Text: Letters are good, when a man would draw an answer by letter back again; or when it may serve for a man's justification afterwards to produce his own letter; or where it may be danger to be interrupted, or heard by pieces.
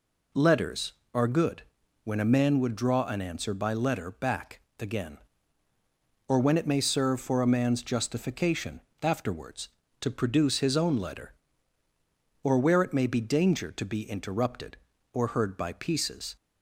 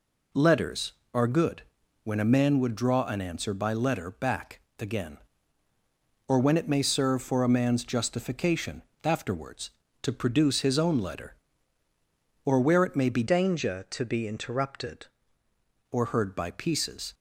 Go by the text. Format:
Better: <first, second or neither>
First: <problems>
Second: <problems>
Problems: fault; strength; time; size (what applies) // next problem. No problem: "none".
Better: first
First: pauses between "back" and "again"; slight; at 4.6 s; 0.18 s long // pauses between "justification" and "afterwards"; slight; at 8.8 s; 0.20 s long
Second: pauses between "back" and "again"; slight; at 4.5 s; 0.18 s long // pauses between "justification" and "afterwards"; slight; at 8.8 s; 0.20 s long // changes voice from "danger" to "interrupted"; from 13.2 to 15.0 s; 1.8 s long